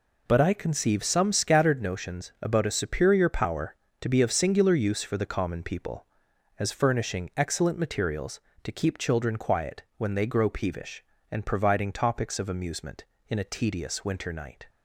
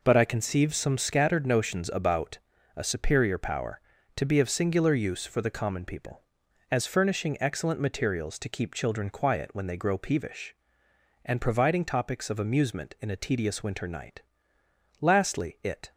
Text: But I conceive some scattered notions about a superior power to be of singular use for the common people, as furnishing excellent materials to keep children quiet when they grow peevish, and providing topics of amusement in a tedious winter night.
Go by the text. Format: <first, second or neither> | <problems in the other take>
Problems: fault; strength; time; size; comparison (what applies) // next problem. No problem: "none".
first | pauses between "about" and "a"; at 2.3 s; 0.38 s long // goes on to say "Lastly it"; noticeable; from 14.9 s on; 0.92 s long